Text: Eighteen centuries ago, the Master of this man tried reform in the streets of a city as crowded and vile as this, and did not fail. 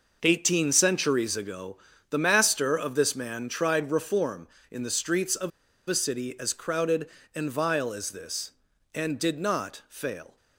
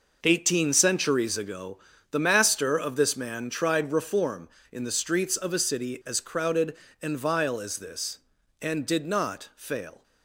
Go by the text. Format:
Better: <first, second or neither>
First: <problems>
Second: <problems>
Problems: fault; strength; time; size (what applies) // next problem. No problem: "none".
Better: second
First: pauses between "of" and "a"; at 5.5 s; 0.39 s long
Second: none